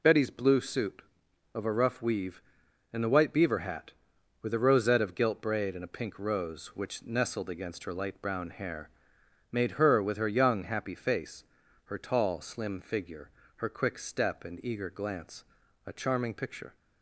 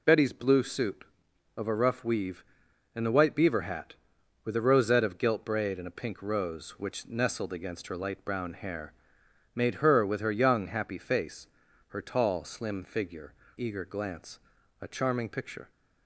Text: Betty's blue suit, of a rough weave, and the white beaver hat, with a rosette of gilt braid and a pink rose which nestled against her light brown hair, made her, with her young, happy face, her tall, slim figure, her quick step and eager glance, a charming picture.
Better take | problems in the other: first | skips "her quick step and"; at 13.4 s

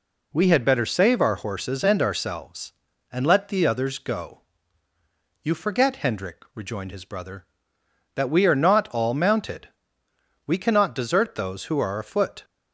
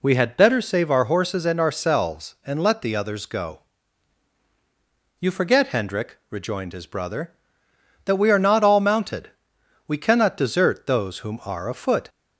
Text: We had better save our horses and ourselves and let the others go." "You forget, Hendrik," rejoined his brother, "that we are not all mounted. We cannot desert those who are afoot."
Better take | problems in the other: first | says "whom" for "who"; at 11.1 s

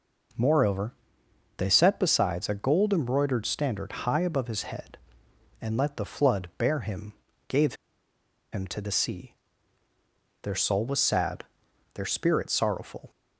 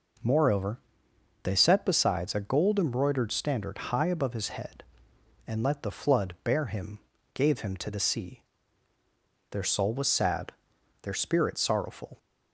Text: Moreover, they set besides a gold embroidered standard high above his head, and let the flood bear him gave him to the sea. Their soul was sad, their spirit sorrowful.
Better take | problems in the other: second | pauses between "him" and "gave"; slight; at 7.1 s; 0.34 s long; slight in the second // pauses between "gave" and "him"; noticeable; at 7.7 s; 0.78 s long

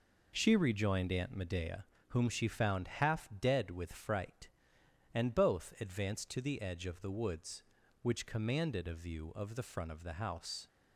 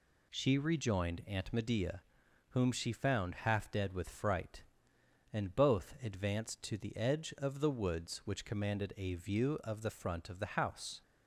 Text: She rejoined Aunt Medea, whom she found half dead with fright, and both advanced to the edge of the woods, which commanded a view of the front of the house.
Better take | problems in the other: neither | none

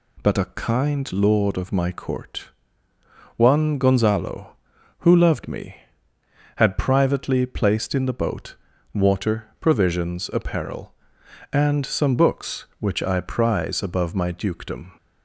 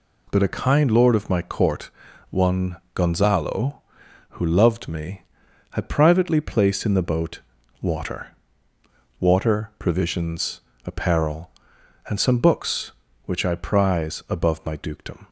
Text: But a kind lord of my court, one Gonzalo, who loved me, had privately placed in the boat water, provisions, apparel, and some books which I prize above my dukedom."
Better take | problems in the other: first | pauses between "one" and "Gonzalo"; slight; at 2.7 s; 0.18 s long // pauses between "boat" and "water"; at 7.4 s; 0.40 s long; slight in the first // says "water" twice; at 9.2 s

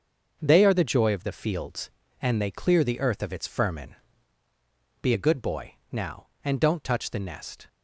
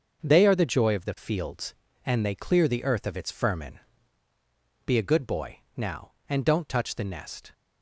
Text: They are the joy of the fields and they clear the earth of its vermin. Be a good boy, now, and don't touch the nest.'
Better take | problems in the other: neither | starts louder than the rest; the same in both

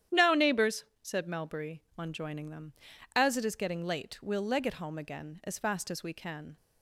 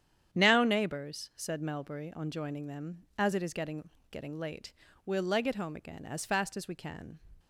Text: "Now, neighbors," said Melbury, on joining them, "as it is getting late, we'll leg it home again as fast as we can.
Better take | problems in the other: first | starts louder than the rest; strong; until 1.4 s; 9 dB; strong in the first // says "getting" twice; at 4.0 s

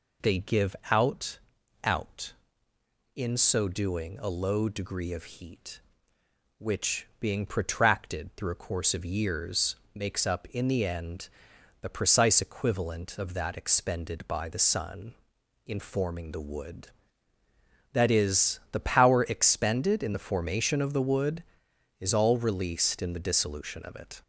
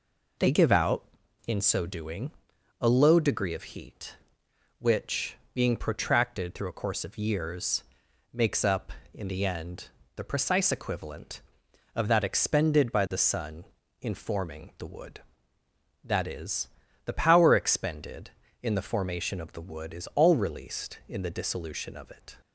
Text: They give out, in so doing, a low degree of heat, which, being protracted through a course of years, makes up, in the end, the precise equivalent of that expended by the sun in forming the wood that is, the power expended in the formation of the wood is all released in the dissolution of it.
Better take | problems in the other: second | says "out" twice; at 1.8 s

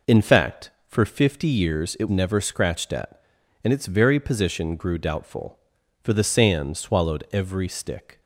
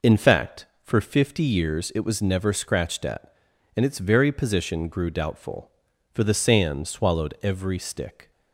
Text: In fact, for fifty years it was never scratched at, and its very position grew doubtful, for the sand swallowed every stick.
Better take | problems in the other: second | skips "was"; at 2.0 s

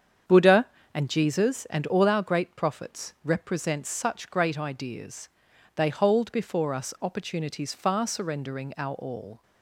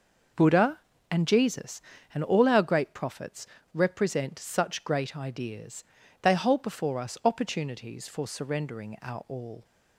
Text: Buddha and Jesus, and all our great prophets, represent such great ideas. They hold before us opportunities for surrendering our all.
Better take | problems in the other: second | starts louder than the rest; strong; until 1.5 s; 8 dB // says "far" for "for"; at 7.7 s

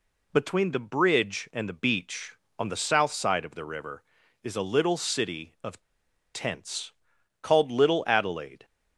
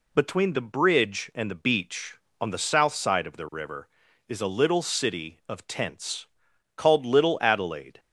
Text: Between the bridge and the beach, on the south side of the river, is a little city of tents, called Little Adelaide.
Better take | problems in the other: second | pauses between "of" and "tents"; noticeable; at 5.8 s; 0.51 s long

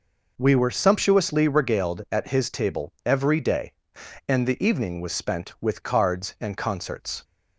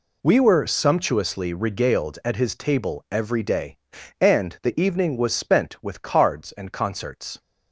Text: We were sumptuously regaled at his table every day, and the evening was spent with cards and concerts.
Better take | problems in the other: neither | none

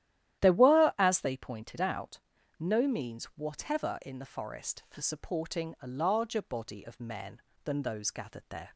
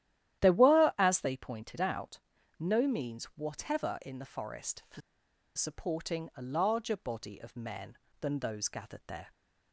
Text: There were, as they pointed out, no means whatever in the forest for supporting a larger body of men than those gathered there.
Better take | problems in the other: first | starts louder than the rest; strong; until 1.4 s; 12 dB; strong in the first // pauses between "for" and "supporting"; noticeable; at 5.0 s; 0.55 s long

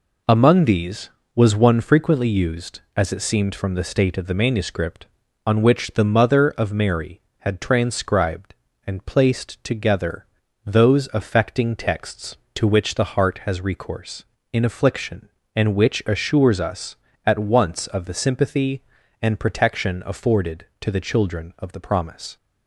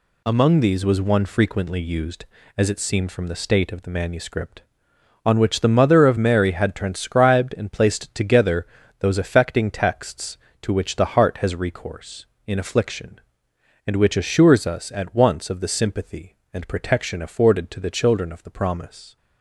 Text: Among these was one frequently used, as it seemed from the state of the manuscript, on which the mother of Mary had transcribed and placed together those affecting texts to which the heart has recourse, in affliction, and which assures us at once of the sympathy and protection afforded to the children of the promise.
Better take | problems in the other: neither | pauses between "together" and "those"; the same in both

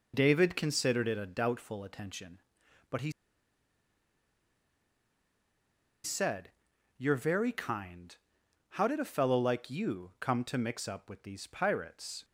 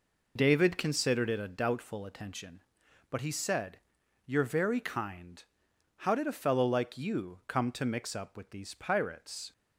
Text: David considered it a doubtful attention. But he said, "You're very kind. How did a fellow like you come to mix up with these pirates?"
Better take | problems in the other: second | pauses between "he" and "said"; strong; at 3.1 s; 2.9 s long

